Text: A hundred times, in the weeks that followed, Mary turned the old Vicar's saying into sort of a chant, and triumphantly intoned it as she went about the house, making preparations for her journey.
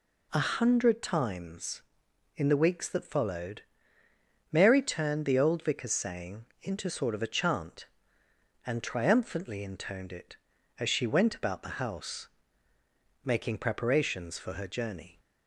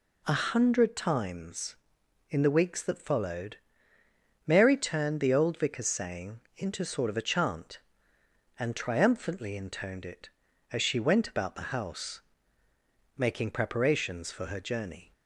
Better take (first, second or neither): neither